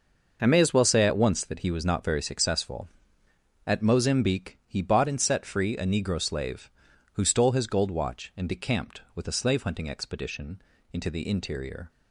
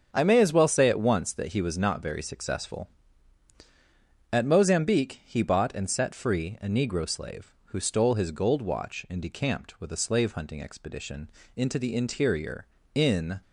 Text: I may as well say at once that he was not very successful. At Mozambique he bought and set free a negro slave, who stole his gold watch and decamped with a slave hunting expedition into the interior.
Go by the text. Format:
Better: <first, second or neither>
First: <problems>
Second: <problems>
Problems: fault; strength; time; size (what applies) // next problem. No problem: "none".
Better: first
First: pauses between "expedition" and "into"; slight; at 10.5 s; 0.32 s long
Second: starts louder than the rest; strong; until 1.1 s; 7 dB // pauses between "expedition" and "into"; slight; at 11.2 s; 0.28 s long // goes on to say "In"; slight; from 12.9 s on; 0.46 s long